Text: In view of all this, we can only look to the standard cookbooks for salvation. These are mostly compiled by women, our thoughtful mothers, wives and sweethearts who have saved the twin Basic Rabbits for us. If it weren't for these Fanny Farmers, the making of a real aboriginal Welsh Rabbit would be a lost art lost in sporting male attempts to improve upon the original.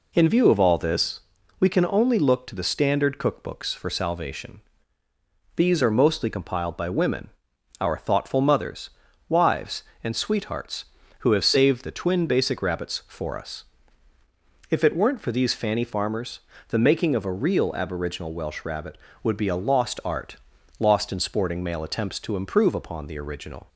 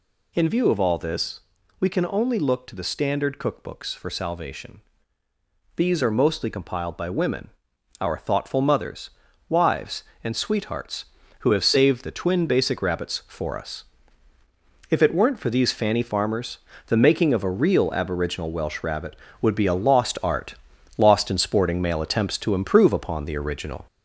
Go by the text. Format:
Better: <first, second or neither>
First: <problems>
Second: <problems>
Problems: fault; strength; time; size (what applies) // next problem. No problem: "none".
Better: first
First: pauses between "art" and "lost"; at 20.3 s; 0.42 s long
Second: gets louder; noticeable; throughout; 4.5 dB // pauses between "art" and "lost"; at 20.5 s; 0.42 s long